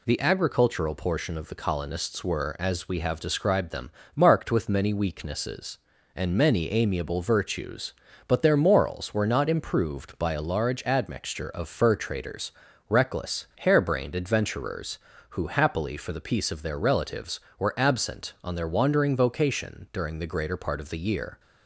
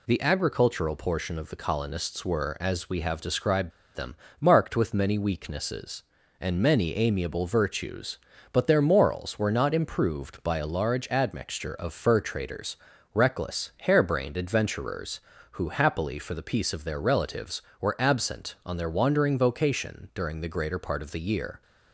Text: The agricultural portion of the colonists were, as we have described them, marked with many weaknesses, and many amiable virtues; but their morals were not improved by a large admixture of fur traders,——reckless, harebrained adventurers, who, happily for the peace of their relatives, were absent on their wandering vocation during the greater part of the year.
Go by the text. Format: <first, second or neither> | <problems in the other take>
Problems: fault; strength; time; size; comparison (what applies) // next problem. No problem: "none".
first | pauses between "described" and "them"; slight; at 3.7 s; 0.24 s long